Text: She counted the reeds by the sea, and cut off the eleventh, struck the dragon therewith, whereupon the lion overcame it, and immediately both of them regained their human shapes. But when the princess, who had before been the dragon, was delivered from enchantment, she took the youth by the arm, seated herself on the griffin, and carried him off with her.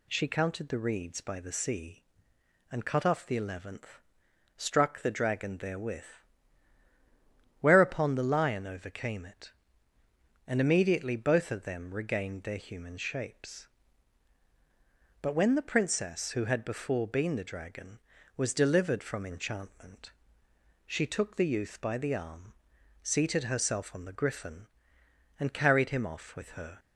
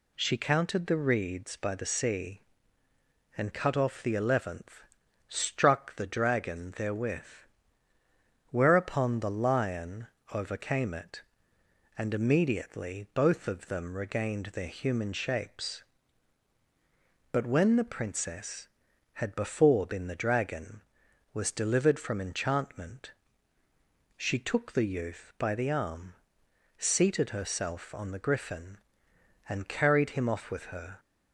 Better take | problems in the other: first | pauses between "lion" and "overcame"; slight; at 10.0 s; 0.24 s long // skips "who"; at 18.9 s

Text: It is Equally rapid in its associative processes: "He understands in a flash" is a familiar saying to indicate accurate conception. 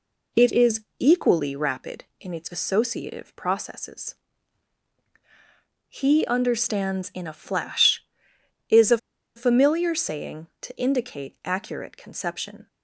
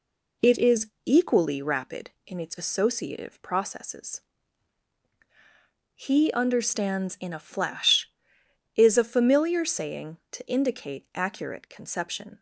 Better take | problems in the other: second | pauses between "is" and "Equally"; slight; at 0.8 s; 0.24 s long; slight in the second // pauses between "a" and "familiar"; at 8.9 s; 0.39 s long

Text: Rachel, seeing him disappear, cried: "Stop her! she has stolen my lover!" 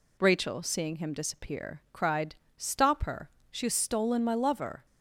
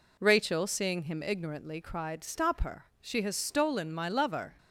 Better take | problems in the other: first | says "ignorantly" for "disappear"; at 1.2 s

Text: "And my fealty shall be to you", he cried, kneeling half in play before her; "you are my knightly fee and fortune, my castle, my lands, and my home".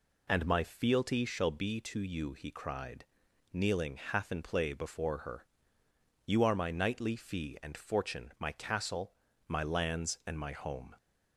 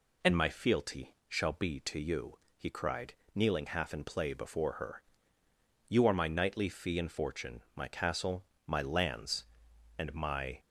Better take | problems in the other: first | stops before "home"; at 10.5 s

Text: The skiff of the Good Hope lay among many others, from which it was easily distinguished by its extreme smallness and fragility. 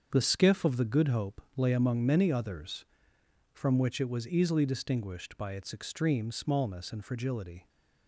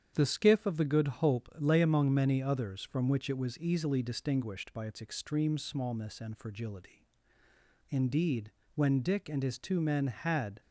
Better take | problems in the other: first | starts louder than the rest; strong; until 1.1 s; 8.5 dB; also in the first // goes on to say "Indeed when Dick and his two men had"; strong; from 7.8 s on; 2.7 s long

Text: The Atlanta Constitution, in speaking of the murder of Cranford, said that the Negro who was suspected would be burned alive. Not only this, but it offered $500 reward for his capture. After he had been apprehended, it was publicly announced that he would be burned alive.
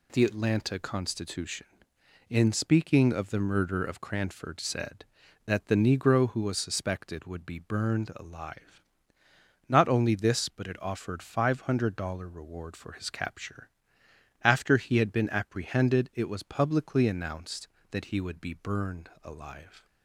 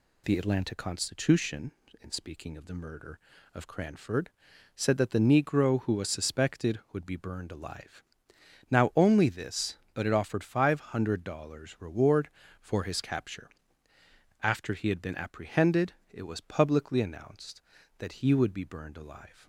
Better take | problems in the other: first | says "Now" for "Not"; at 8.7 s

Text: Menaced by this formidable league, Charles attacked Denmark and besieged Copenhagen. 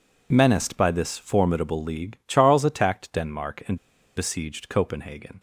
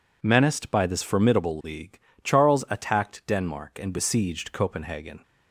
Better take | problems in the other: second | pauses between "and" and "besieged"; at 3.7 s; 0.39 s long

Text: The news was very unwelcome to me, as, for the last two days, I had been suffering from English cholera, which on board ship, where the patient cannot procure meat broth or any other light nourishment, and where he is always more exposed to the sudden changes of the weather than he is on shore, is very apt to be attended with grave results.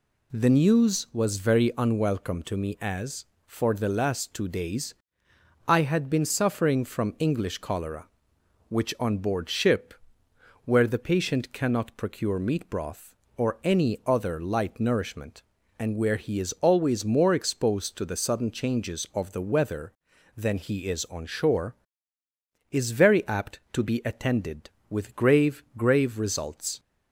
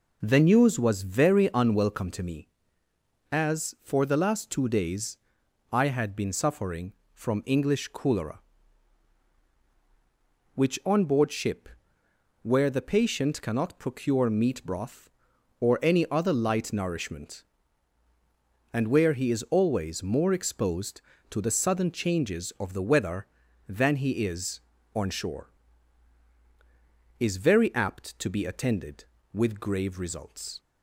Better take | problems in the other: second | says "grave" twice; at 25.7 s

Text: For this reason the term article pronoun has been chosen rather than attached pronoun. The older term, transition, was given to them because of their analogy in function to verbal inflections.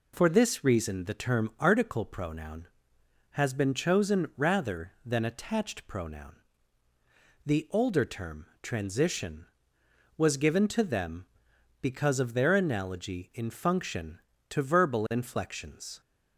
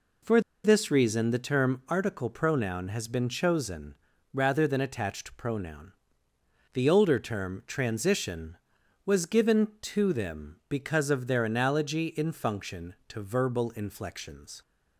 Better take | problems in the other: first | pauses between "For" and "this"; slight; at 0.3 s; 0.24 s long // pauses between "chosen" and "rather"; slight; at 3.9 s; 0.36 s long

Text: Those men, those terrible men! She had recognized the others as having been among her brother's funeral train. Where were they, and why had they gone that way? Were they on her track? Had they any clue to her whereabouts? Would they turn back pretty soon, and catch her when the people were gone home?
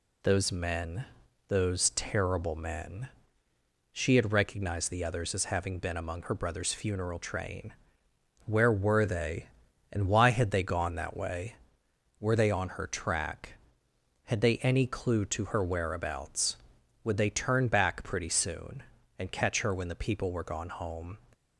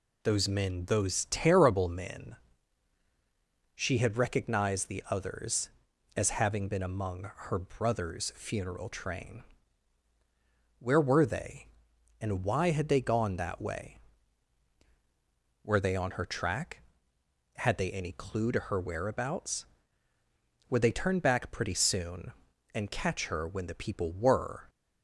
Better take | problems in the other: first | stops before "gone home"; at 24.6 s

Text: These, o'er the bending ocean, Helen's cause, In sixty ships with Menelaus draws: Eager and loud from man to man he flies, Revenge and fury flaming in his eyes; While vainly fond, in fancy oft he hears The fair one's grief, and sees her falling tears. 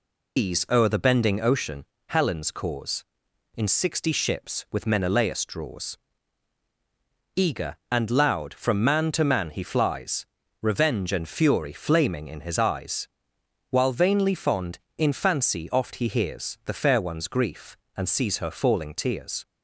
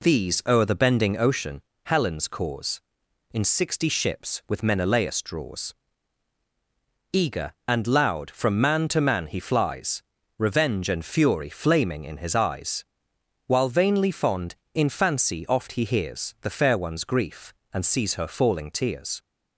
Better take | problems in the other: second | loses the start of "These"; at 0.3 s; 120 ms

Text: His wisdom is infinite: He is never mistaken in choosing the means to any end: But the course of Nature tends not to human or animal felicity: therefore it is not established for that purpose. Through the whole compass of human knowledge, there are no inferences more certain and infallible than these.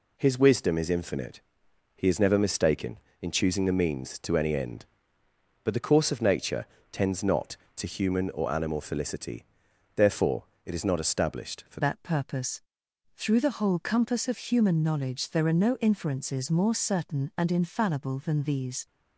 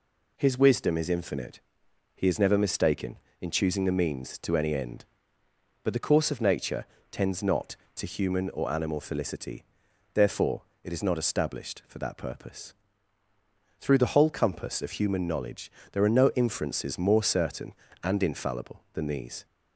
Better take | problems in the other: second | pauses between "Nature" and "tends"; slight; at 6.6 s; 0.26 s long; slight in the second // pauses between "therefore" and "it"; slight; at 10.4 s; 0.20 s long; slight in the second // changes voice at "that"; from 11.8 s on; 7.0 s long

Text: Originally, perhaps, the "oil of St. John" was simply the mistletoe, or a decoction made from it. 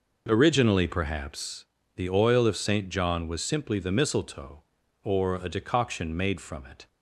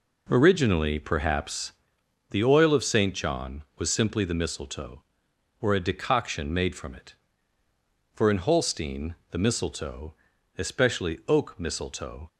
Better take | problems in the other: first | goes on to say "For in Holstein the mistletoe especially oak mistletoe"; strong; from 8.1 s on; 4.1 s long

